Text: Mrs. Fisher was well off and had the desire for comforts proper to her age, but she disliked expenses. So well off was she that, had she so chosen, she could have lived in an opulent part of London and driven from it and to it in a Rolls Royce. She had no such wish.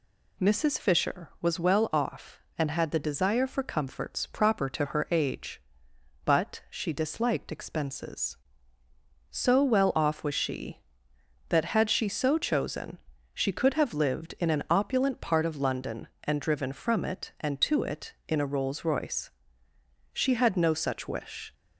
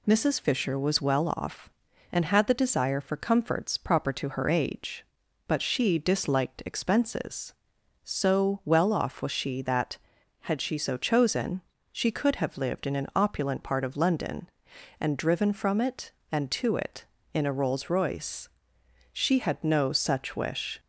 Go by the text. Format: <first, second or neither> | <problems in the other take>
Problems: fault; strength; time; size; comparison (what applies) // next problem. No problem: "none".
neither | none